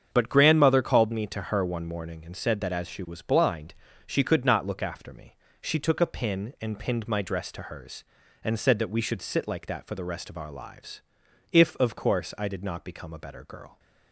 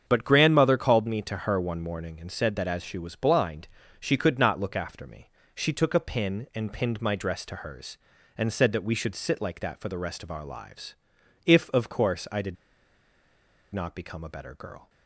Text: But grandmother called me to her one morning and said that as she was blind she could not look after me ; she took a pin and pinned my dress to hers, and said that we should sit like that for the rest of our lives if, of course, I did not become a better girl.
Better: first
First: starts louder than the rest; strong; until 1.1 s; 7.5 dB // pauses between "blind" and "she"; slight; at 3.7 s; 0.32 s long // pauses between "lives" and "if"; noticeable; at 11.0 s; 0.52 s long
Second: starts louder than the rest; strong; until 1.0 s; 7.5 dB // pauses between "blind" and "she"; slight; at 3.6 s; 0.32 s long // pauses between "lives" and "if"; noticeable; at 10.9 s; 0.52 s long // pauses between "did" and "not"; at 12.5 s; 1.2 s long

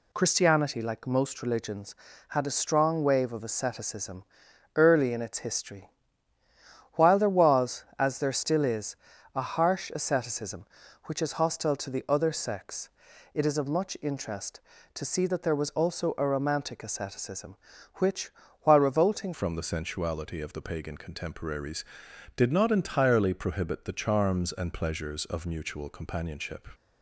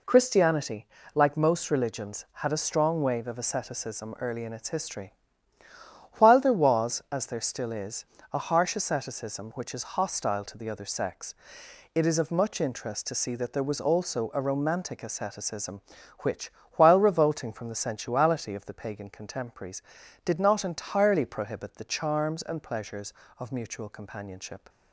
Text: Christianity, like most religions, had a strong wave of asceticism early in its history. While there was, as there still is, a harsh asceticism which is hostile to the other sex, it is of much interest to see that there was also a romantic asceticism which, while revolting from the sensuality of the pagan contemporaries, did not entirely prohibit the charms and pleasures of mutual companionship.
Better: second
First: pauses between "asceticism" and "early"; noticeable; at 4.2 s; 0.50 s long // changes voice at "from"; from 19.3 s on; 7.3 s long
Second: none

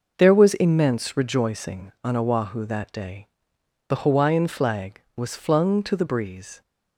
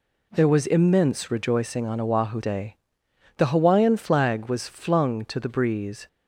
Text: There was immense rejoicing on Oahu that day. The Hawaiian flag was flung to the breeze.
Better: first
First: none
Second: skips "that"; at 2.4 s

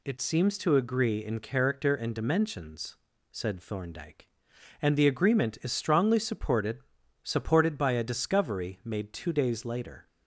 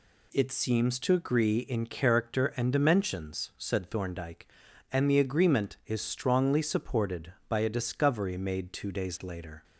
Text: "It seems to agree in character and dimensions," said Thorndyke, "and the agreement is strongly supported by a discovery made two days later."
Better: second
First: says "supported" twice; at 7.2 s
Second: none

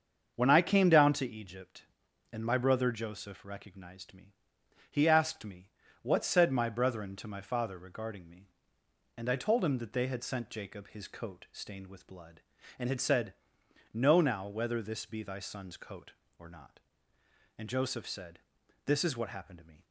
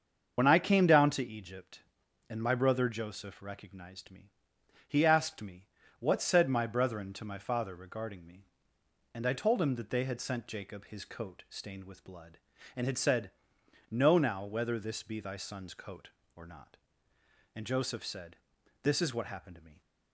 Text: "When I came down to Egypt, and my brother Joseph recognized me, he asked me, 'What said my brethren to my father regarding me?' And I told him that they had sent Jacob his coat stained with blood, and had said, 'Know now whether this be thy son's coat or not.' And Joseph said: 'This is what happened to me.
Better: first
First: starts louder than the rest; until 1.3 s; 7 dB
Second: loses the start of "When"; at 0.3 s; 55 ms // starts louder than the rest; until 1.3 s; 7 dB

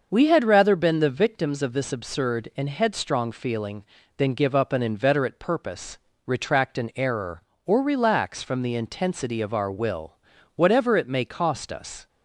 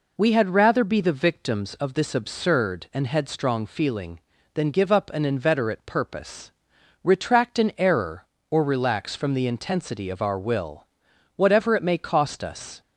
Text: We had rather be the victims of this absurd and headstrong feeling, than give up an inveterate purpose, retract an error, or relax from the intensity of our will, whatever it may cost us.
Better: second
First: starts louder than the rest; until 1.1 s; 6.5 dB // says "been" for "be"; at 0.7 s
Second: none

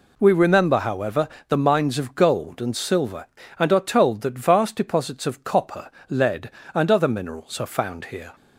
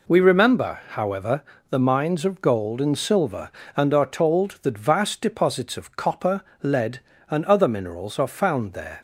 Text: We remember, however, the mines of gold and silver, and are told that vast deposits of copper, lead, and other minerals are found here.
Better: first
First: none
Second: says "there" for "here"; at 8.7 s

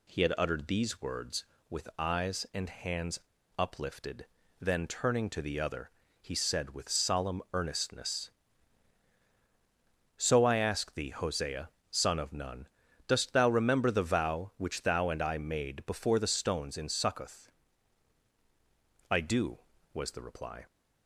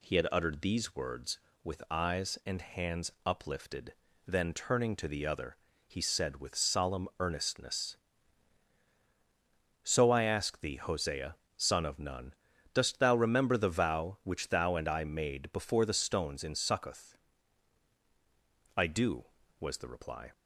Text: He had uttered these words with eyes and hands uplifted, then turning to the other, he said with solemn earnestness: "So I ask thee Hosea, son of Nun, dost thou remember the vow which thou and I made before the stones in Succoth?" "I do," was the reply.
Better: second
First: pauses between "hands" and "uplifted"; at 3.2 s; 0.38 s long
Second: none

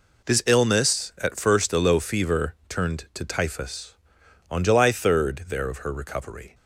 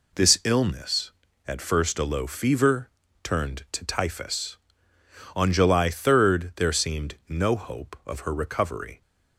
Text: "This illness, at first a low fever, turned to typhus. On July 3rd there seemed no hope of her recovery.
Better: second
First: skips "seemed no hope"; at 5.6 s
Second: none

